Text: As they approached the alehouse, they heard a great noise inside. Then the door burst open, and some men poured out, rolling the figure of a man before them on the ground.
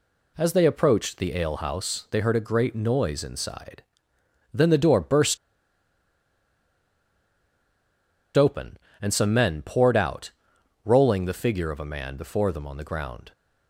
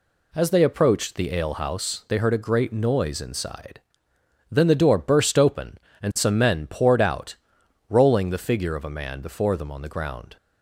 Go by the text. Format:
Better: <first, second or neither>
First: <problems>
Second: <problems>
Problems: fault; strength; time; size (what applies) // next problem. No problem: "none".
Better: second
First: pauses between "burst" and "open"; strong; at 5.3 s; 2.9 s long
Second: none